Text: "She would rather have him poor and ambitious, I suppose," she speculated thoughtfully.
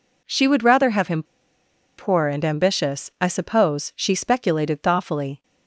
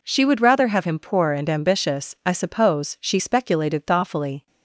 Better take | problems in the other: second | pauses between "him" and "poor"; noticeable; at 1.2 s; 0.74 s long

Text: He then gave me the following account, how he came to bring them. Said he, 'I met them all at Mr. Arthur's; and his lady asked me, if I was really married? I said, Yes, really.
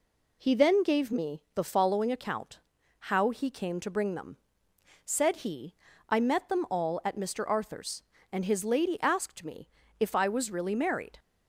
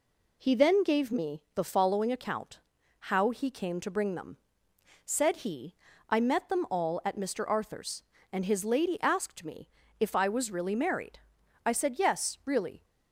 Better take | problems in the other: second | stops before "I said Yes really"; at 11.1 s

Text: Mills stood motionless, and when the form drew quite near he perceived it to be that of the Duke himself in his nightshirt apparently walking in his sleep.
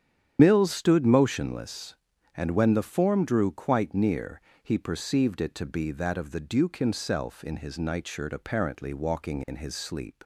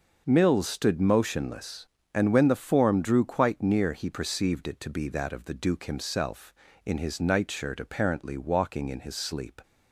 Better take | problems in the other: second | loses the start of "Mills"; at 0.3 s; 85 ms // starts louder than the rest; strong; until 1.4 s; 9.5 dB // pauses between "near" and "he"; slight; at 4.4 s; 0.20 s long

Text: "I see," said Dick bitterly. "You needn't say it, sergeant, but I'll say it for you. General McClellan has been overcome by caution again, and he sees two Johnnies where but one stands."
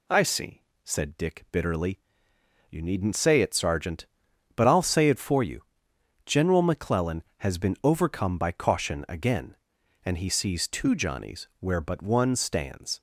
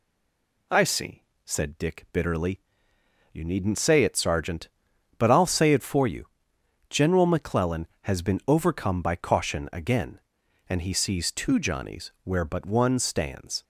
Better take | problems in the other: first | stays silent before the first word; slight; until 0.6 s; 0.6 s long

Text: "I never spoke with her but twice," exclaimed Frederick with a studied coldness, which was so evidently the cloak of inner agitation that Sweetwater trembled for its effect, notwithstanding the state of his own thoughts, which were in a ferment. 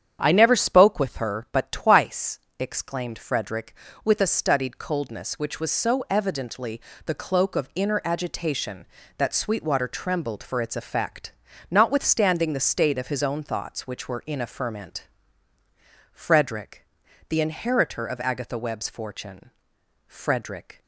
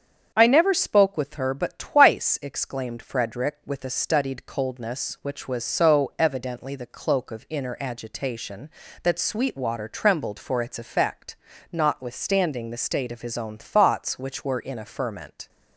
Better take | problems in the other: second | starts louder than the rest; strong; until 1.2 s; 8.5 dB; strong in the second // pauses between "evidently" and "the"; slight; at 6.7 s; 0.28 s long // goes on to say "Frederick the inheritor of Agatha Webb's fortune Frederick"; strong; from 16.1 s on; 4.7 s long

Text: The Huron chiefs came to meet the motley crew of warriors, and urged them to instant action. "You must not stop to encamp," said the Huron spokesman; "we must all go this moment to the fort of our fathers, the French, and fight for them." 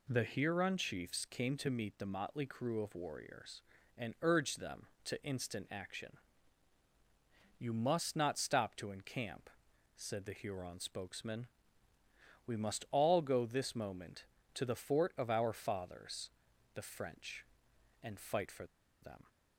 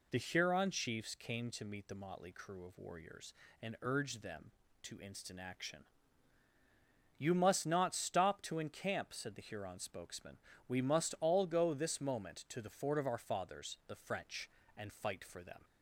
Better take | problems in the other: second | pauses between "for" and "them"; slight; at 18.6 s; 0.35 s long

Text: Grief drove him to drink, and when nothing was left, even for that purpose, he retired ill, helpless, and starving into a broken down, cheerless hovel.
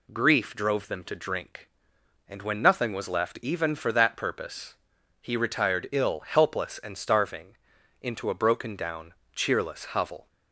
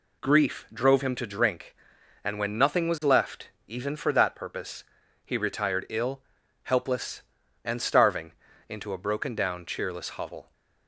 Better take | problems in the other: second | says "them" for "him"; at 0.8 s // pauses between "starving" and "into"; noticeable; at 7.5 s; 0.46 s long; also in the second

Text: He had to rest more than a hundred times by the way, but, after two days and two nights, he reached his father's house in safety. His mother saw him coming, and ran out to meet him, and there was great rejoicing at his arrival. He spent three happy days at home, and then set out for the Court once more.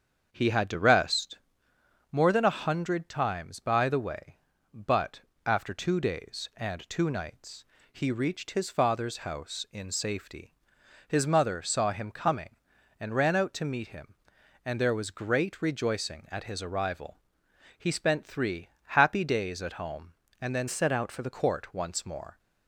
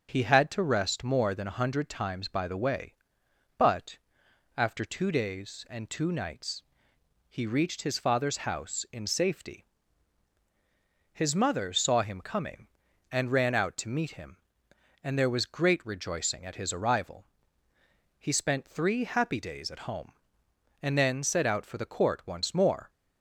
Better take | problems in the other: second | starts louder than the rest; strong; until 1.3 s; 7.5 dB; also in the second // pauses between "rest" and "more"; noticeable; at 1.3 s; 0.74 s long // pauses between "three" and "happy"; slight; at 18.6 s; 0.18 s long // changes voice from "set" to "the"; from 20.6 to 21.2 s; 0.6 s long

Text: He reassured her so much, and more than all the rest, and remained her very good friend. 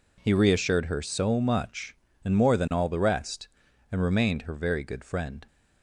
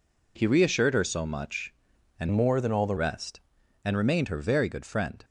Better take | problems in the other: first | changes voice from "more" to "the"; from 2.3 to 2.9 s; 0.6 s long

